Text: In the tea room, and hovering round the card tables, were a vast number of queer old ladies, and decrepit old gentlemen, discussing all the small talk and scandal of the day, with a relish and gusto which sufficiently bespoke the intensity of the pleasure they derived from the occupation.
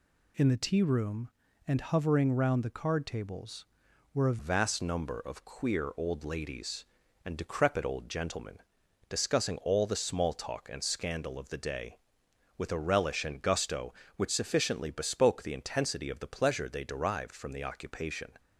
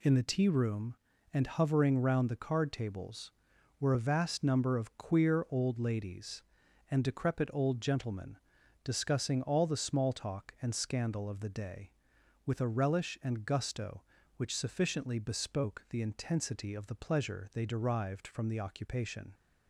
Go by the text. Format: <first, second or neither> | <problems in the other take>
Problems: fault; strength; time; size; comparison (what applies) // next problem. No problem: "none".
second | changes voice at "vast"; from 4.3 s on; 14.0 s long